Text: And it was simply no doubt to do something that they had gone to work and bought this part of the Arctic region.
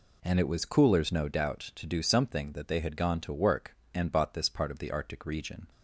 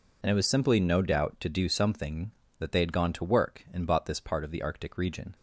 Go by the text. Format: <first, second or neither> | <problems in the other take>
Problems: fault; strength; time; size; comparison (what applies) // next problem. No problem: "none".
second | says "coolers" for "simply"; at 0.6 s